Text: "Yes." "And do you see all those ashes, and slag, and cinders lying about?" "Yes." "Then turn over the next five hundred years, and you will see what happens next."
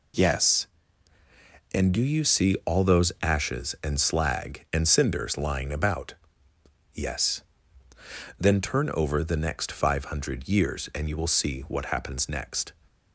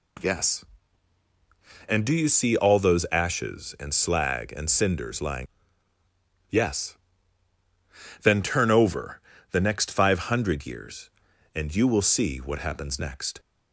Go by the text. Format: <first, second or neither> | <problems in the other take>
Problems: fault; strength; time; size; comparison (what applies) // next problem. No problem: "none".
first | skips "about"; at 5.9 s // pauses between "over" and "the"; slight; at 9.2 s; 0.30 s long